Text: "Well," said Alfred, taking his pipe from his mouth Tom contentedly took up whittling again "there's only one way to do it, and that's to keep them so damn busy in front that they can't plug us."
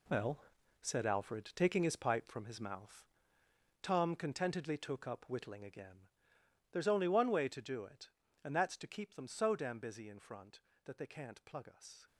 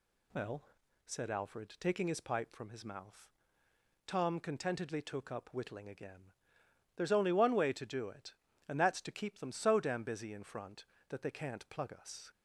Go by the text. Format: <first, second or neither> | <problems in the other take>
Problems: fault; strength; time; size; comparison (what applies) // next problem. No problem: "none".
second | gets quieter; strong; throughout; 11.5 dB // pauses between "mouth" and "Tom"; noticeable; at 3.0 s; 0.78 s long; noticeable in the second // pauses between "again" and "there's"; noticeable; at 6.0 s; 0.62 s long; noticeable in the second